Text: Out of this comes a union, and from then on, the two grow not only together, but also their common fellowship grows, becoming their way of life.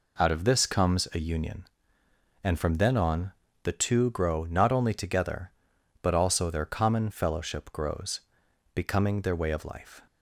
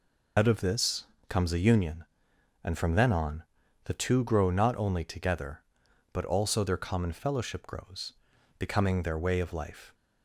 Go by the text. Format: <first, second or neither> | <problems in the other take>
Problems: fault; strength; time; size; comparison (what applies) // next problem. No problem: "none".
first | loses the start of "Out"; at 0.3 s; 70 ms // pauses between "this" and "comes"; slight; at 1.0 s; 0.20 s long